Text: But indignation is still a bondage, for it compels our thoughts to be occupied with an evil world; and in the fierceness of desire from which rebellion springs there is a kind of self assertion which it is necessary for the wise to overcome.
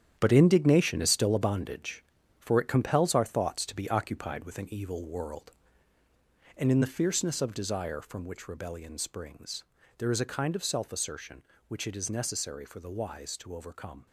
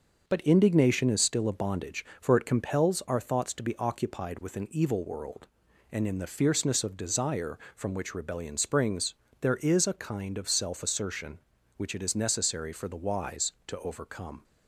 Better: second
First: gets quieter; strong; throughout; 9.5 dB // starts louder than the rest; strong; until 1.1 s; 9.5 dB // pauses between "springs" and "there"; slight; at 9.6 s; 0.32 s long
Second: starts louder than the rest; until 1.2 s; 6 dB // pauses between "springs" and "there"; slight; at 9.1 s; 0.26 s long

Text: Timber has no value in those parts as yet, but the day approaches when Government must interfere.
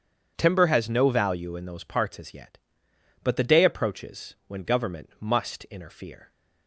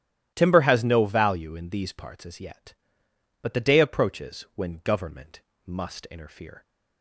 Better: first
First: starts louder than the rest; strong; until 1.3 s; 8 dB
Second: starts louder than the rest; strong; until 1.3 s; 13.5 dB // says "these" for "those"; at 1.6 s // pauses between "Government" and "must"; slight; at 5.4 s; 0.26 s long

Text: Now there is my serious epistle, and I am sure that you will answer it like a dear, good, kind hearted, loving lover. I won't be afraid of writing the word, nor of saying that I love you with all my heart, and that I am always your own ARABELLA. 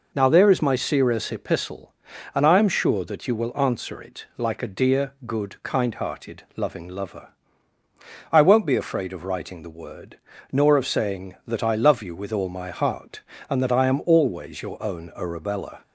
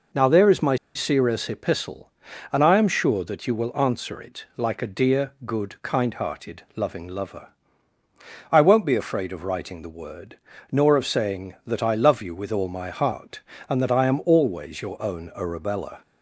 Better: first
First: none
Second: pauses between "my" and "serious"; slight; at 0.7 s; 0.19 s long

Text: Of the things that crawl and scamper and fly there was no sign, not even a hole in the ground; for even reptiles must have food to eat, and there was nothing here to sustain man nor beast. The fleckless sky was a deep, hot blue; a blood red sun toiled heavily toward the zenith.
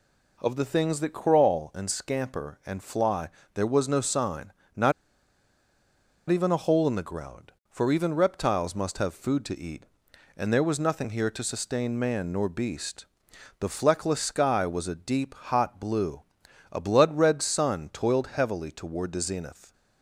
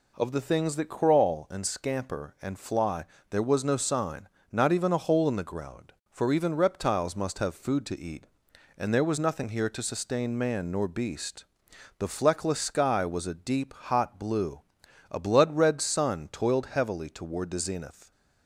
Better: second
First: pauses between "fly" and "there"; slight; at 3.2 s; 0.26 s long // pauses between "not" and "even"; strong; at 4.9 s; 1.3 s long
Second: pauses between "fly" and "there"; slight; at 3.0 s; 0.26 s long

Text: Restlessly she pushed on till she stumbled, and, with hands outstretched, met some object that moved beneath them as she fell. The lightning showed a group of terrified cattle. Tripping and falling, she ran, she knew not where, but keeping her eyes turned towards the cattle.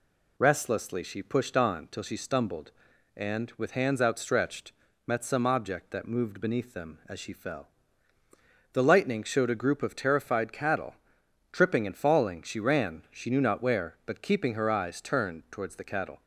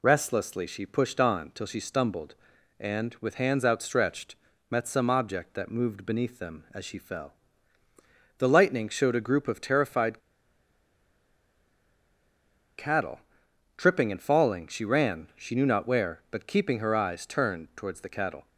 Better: first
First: none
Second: pauses between "terrified" and "cattle"; strong; at 10.1 s; 2.5 s long

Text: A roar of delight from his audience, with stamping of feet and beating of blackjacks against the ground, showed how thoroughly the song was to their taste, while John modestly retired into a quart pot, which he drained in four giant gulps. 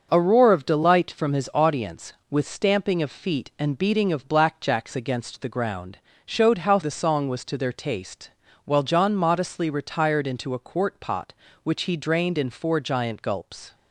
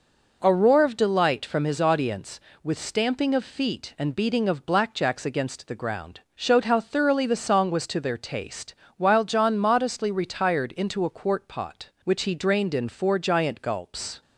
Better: second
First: starts louder than the rest; noticeable; until 1.1 s; 6 dB // skips "thoroughly"; at 6.8 s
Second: none

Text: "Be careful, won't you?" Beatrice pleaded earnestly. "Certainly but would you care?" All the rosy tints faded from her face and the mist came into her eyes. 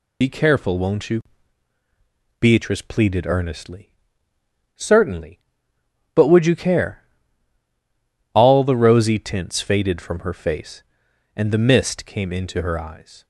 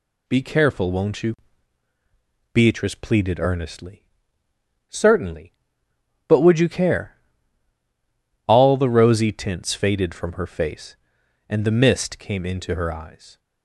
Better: second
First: loses the start of "Be"; at 0.2 s; 55 ms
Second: none

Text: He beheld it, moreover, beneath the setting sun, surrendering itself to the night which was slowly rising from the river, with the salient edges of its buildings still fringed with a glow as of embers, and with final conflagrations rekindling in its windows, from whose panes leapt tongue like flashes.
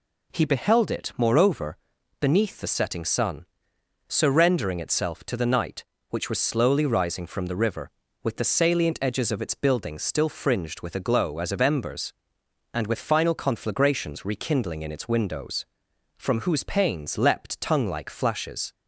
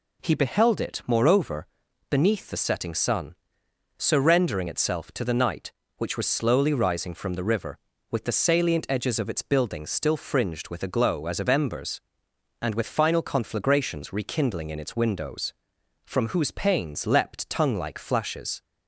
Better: neither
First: none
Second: none

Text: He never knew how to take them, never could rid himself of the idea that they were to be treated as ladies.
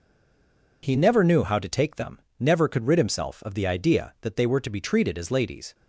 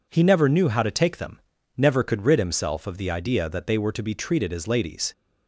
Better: second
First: stays silent before the first word; slight; until 0.8 s; 0.8 s long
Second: none

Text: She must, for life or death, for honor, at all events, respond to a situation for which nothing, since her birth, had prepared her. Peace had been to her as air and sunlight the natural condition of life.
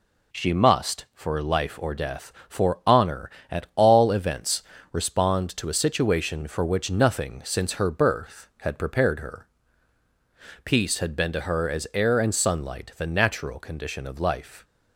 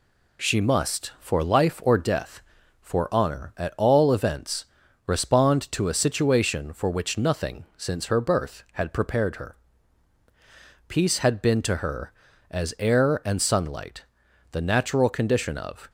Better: first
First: none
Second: pauses between "sunlight" and "the"; noticeable; at 14.0 s; 0.46 s long // stops before "life"; at 15.8 s

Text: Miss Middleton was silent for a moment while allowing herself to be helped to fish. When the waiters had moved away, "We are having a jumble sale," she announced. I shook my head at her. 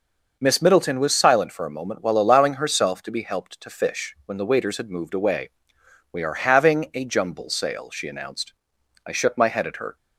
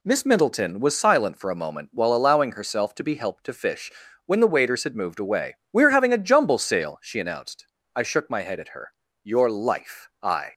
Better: first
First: none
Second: goes on to say "Your life I"; noticeable; from 9.2 s on; 1.3 s long

